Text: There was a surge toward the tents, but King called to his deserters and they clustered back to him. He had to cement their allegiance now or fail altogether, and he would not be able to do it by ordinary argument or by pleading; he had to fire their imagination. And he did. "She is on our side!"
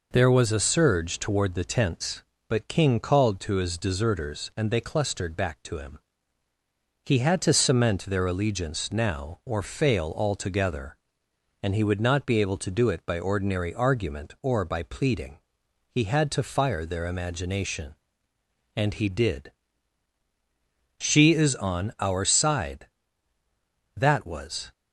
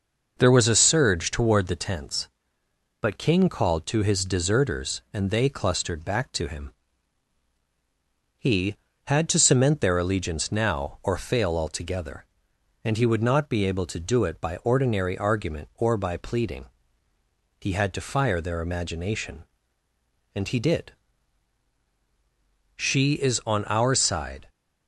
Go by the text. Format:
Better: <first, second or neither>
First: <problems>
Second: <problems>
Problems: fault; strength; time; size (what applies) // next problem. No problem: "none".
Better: second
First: goes on to say "That was"; noticeable; from 23.9 s on; 0.76 s long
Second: none